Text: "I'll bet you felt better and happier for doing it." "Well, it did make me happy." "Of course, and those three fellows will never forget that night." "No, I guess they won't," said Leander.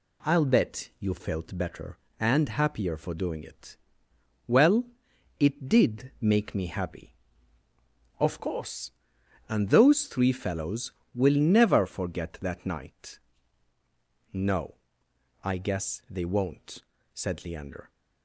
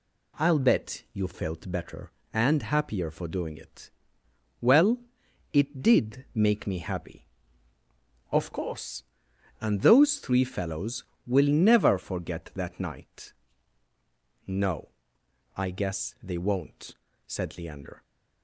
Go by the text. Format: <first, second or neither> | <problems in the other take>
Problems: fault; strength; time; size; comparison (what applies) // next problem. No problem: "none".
neither | none